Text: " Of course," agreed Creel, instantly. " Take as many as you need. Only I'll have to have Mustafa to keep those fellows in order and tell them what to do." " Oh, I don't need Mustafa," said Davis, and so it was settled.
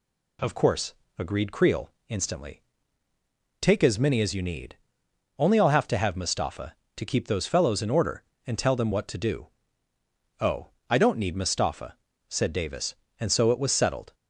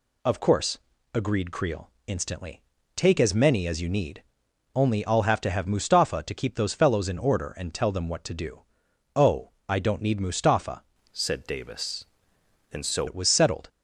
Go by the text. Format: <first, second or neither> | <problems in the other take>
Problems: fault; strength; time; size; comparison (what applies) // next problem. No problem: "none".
first | changes voice from "said" to "so"; from 11.1 to 13.0 s; 1.9 s long